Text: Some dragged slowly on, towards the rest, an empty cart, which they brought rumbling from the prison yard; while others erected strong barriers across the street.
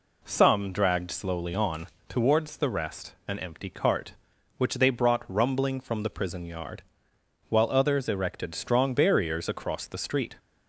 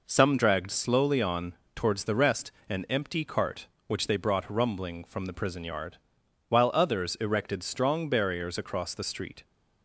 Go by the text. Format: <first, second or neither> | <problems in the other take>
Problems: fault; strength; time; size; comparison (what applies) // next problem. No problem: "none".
neither | none